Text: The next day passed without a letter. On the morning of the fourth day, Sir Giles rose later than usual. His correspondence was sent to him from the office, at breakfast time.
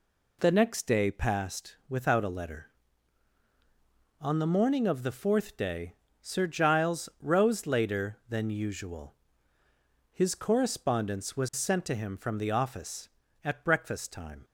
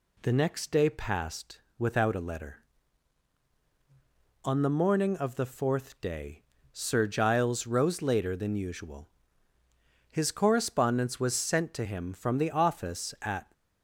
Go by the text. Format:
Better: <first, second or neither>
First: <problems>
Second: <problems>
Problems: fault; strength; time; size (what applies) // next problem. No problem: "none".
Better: first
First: none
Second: pauses between "passed" and "without"; slight; at 1.5 s; 0.18 s long // stops before "breakfast time"; at 13.5 s